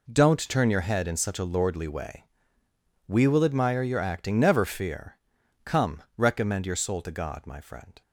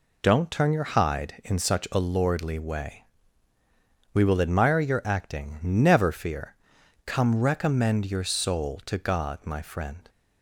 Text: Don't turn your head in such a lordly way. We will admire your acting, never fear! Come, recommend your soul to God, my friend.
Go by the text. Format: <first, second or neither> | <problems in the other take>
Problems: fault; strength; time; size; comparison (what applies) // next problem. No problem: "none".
first | says "hide" for "head"; at 0.8 s